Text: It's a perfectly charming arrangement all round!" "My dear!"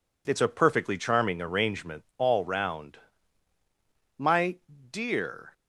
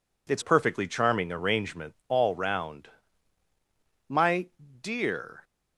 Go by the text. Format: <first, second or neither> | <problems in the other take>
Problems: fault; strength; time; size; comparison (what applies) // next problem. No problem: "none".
first | skips "a"; at 0.4 s // pauses between "My" and "dear"; slight; at 4.4 s; 0.36 s long; slight in the first